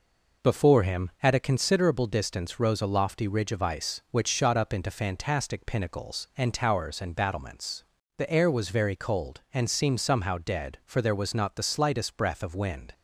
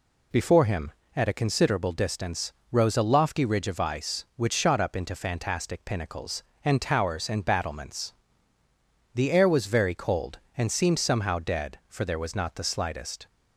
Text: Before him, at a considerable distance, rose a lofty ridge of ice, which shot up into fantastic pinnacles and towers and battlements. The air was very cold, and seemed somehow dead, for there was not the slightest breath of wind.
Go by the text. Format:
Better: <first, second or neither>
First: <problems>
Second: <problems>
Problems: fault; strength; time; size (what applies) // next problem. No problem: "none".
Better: first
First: none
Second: stops before "breath of wind"; at 13.2 s